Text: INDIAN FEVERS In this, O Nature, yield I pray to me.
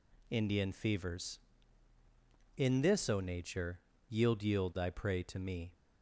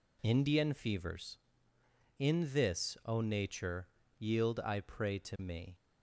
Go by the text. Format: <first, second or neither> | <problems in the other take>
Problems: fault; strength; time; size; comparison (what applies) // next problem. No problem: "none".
second | says "yield" twice; at 4.4 s